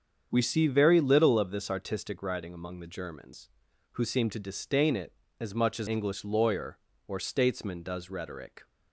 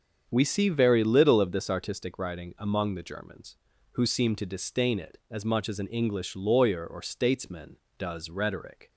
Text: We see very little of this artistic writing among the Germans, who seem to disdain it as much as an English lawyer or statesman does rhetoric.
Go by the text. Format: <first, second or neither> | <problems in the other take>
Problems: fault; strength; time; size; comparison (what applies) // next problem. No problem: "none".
second | starts louder than the rest; strong; until 1.3 s; 7.5 dB; also in the second // skips "an"; at 5.8 s